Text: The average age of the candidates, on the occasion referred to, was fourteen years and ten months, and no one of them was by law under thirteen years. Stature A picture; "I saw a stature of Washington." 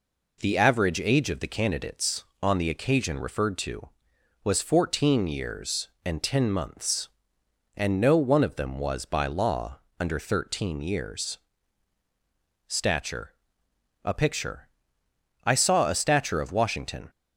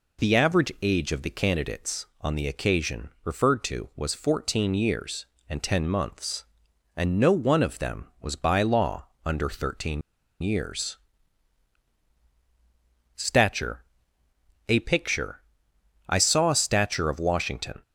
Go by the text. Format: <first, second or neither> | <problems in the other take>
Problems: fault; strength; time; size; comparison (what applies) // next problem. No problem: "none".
first | pauses between "occasion" and "referred"; slight; at 3.0 s; 0.16 s long // pauses between "law" and "under"; slight; at 9.0 s; 0.16 s long; slight in the first // pauses between "thirteen" and "years"; at 10.0 s; 0.41 s long // pauses between "Stature" and "A"; noticeable; at 13.8 s; 0.82 s long; noticeable in the first